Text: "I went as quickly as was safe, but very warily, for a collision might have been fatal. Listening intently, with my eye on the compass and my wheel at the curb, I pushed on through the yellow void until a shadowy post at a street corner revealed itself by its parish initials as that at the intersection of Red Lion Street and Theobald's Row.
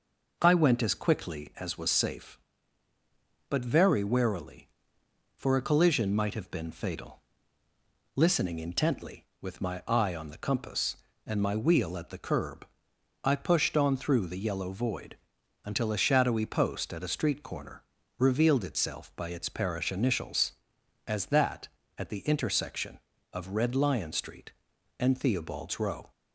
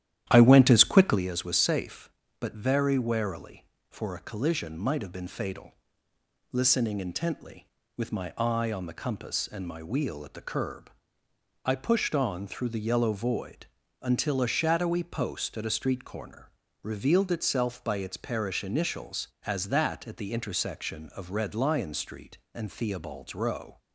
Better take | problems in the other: first | starts louder than the rest; strong; until 1.2 s; 12 dB // pauses between "void" and "until"; slight; at 13.6 s; 0.36 s long; noticeable in the first // pauses between "corner" and "revealed"; slight; at 16.5 s; 0.32 s long; slight in the first

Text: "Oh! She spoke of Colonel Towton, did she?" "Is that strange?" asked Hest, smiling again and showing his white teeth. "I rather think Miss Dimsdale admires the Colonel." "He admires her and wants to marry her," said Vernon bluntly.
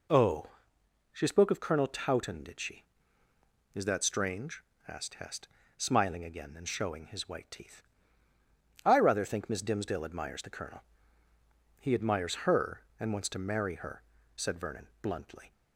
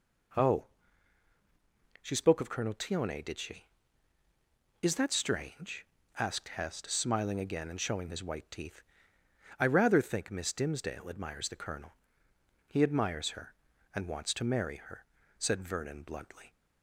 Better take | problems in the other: first | says "Tione" for "Towton"; at 2.7 s

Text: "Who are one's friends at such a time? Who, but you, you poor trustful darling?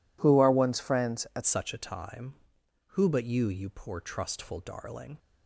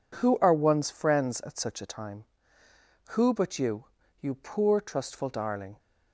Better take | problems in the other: second | changes voice at "such"; from 1.4 s on; 3.7 s long

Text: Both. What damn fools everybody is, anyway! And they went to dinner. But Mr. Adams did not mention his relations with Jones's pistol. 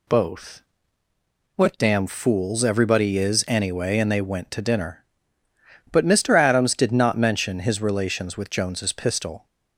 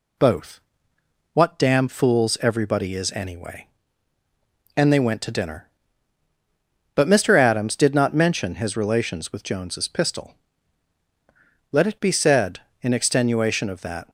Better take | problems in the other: first | goes on to say "Let it be said in extenuation of that"; strong; from 11.7 s on; 2.3 s long

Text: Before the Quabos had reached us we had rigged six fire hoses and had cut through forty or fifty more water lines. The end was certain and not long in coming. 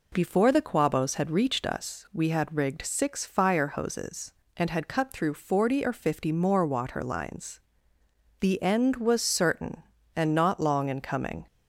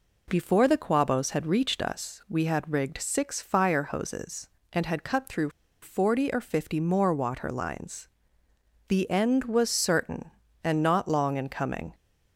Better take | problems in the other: first | pauses between "through" and "forty"; slight; at 5.4 s; 0.33 s long

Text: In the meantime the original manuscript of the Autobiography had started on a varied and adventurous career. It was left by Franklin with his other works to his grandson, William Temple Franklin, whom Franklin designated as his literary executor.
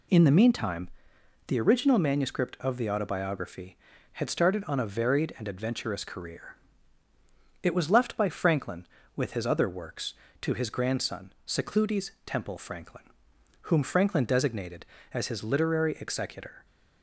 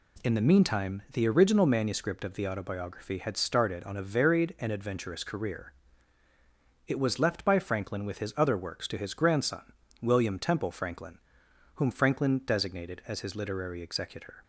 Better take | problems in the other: second | pauses between "meantime" and "the"; noticeable; at 0.8 s; 0.58 s long // says "Secludes" for "William"; at 11.4 s

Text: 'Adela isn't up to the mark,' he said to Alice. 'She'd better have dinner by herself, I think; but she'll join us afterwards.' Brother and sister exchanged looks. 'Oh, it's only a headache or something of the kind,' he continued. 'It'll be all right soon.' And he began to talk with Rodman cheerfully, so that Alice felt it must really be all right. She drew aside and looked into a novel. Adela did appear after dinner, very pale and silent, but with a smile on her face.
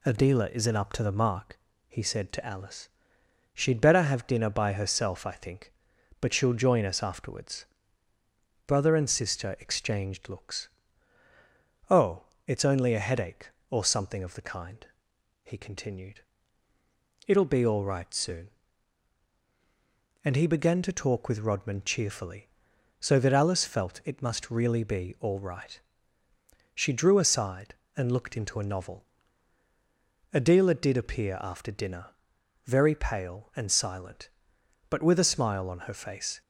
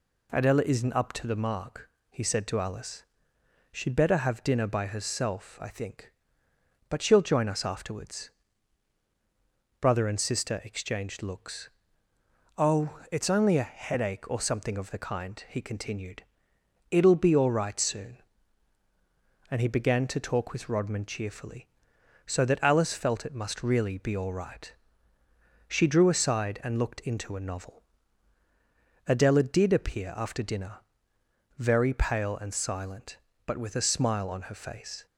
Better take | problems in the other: neither | none

